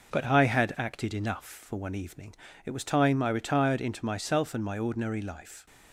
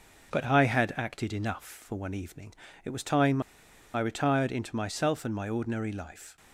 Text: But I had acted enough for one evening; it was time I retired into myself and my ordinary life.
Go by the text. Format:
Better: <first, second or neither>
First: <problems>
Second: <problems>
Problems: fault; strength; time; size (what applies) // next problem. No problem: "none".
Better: first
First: none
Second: pauses between "time" and "I"; noticeable; at 3.4 s; 0.53 s long